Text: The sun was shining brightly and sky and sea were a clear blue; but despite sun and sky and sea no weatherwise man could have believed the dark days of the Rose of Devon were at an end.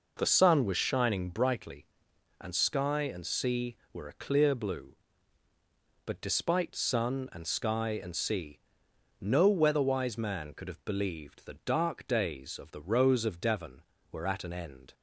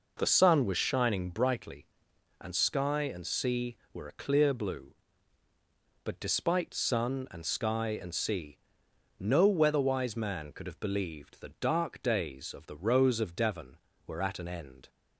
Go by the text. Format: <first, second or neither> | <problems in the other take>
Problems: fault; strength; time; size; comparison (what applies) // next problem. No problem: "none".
neither | pauses between "sea" and "no"; noticeable; the same in both